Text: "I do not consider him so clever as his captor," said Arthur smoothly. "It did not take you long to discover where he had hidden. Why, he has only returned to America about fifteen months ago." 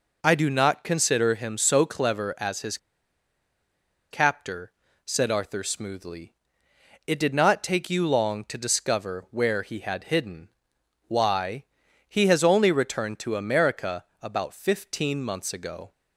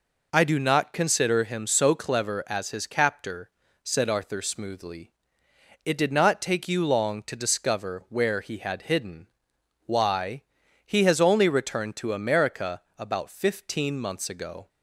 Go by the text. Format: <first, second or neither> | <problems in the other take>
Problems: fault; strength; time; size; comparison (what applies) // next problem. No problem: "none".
second | pauses between "his" and "captor"; strong; at 2.7 s; 1.3 s long // pauses between "America" and "about"; slight; at 14.0 s; 0.18 s long; slight in the second